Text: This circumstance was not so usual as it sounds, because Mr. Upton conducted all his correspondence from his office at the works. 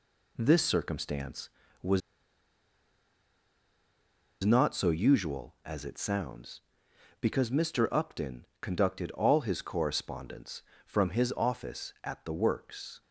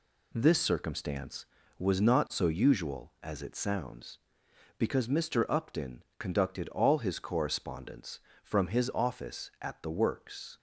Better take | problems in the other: second | pauses between "was" and "not"; strong; at 2.0 s; 2.4 s long // pauses between "Upton" and "conducted"; slight; at 8.4 s; 0.16 s long; slight in the second

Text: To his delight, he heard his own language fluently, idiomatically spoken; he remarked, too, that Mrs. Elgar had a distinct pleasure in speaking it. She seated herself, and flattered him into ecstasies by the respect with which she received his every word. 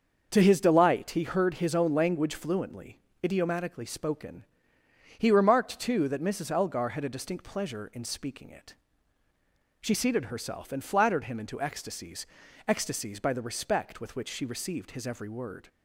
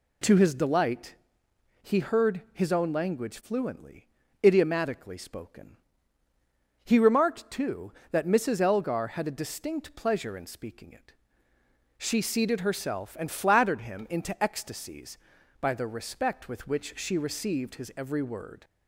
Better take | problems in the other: second | starts louder than the rest; until 1.3 s; 6.5 dB // says "ecstasies" twice; at 12.6 s

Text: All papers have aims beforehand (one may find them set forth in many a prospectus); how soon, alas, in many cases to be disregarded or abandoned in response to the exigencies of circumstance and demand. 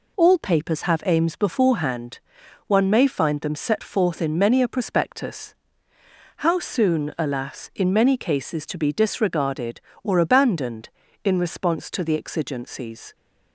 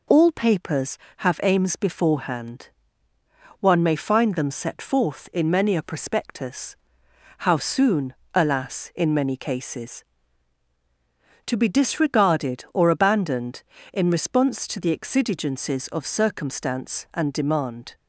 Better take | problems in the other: second | stops before "of circumstance and demand"; at 13.1 s

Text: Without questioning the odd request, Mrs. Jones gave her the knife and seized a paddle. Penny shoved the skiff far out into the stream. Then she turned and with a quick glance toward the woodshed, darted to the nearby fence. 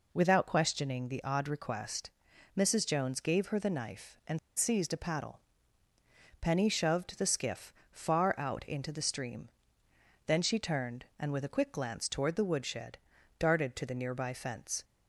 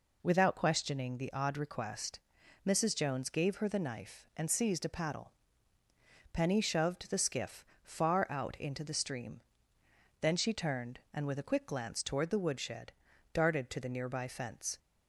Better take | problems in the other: second | pauses between "and" and "seized"; slight; at 4.3 s; 0.18 s long // pauses between "skiff" and "far"; slight; at 7.7 s; 0.18 s long; slight in the second

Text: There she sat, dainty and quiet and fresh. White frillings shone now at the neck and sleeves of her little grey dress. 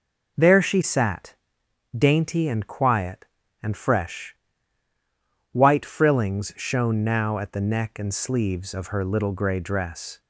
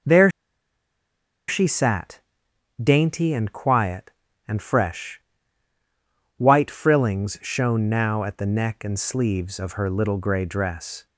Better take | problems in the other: first | pauses between "There" and "she"; at 0.3 s; 1.1 s long

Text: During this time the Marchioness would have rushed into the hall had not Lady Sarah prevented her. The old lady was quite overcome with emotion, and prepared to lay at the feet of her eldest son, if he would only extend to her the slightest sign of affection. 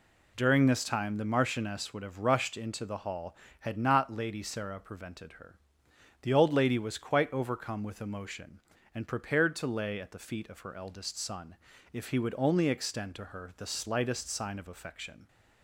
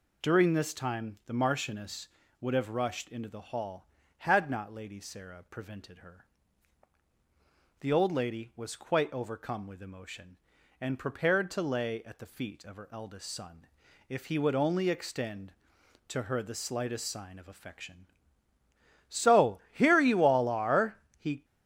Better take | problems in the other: first | goes on to say "So here you all are he"; strong; from 19.0 s on; 2.3 s long

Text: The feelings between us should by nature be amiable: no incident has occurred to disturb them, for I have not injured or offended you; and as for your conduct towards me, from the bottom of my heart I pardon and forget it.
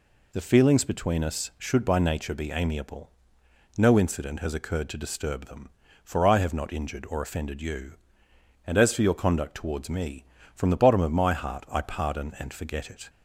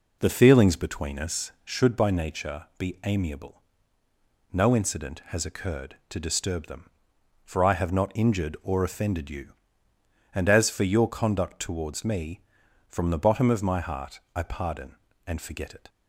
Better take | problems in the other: first | starts louder than the rest; noticeable; until 1.8 s; 4 dB // pauses between "heart" and "I"; slight; at 14.1 s; 0.16 s long

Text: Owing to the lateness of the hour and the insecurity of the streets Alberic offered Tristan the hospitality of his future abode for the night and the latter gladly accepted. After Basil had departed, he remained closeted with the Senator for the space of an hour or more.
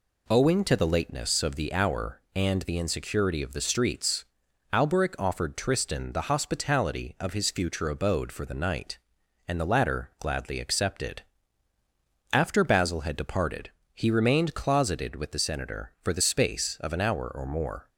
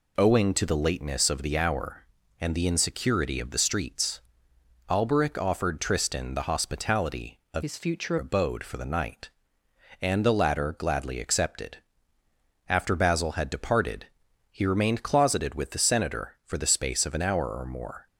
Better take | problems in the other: first | pauses between "streets" and "Alberic"; noticeable; at 4.1 s; 0.70 s long; noticeable in the first // changes voice from "his" to "future"; from 7.6 to 8.1 s; 0.5 s long

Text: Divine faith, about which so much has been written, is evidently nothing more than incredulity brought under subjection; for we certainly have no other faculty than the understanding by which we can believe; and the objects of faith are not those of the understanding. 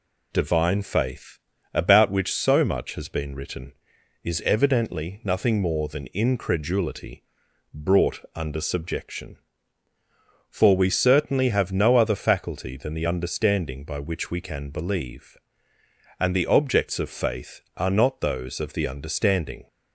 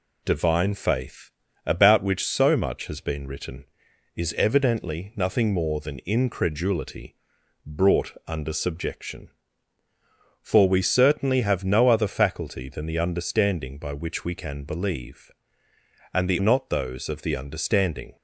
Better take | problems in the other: first | pauses between "incredulity" and "brought"; noticeable; at 7.1 s; 0.50 s long; noticeable in the first // skips "objects of faith are"; at 16.3 s

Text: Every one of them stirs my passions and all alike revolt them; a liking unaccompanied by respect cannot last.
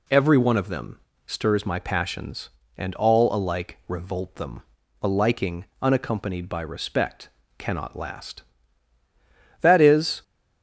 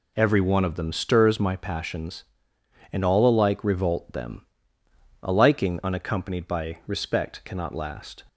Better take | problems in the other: second | pauses between "them" and "stirs"; slight; at 0.9 s; 0.28 s long // pauses between "liking" and "unaccompanied"; slight; at 5.6 s; 0.18 s long // goes on to say "That is"; from 9.6 s on; 0.60 s long

